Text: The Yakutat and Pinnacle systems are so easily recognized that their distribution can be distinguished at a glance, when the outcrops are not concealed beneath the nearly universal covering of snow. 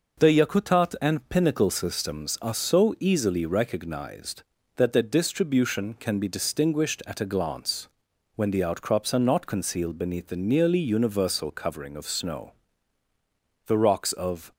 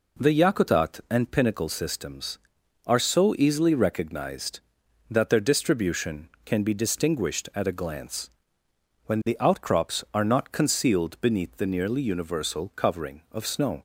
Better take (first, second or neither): second